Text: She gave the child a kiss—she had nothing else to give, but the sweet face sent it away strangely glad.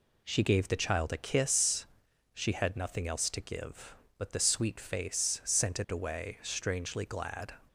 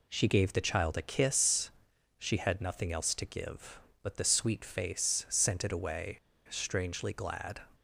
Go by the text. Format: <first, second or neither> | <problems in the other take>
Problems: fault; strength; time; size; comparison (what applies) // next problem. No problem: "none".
first | pauses between "away" and "strangely"; slight; at 6.1 s; 0.30 s long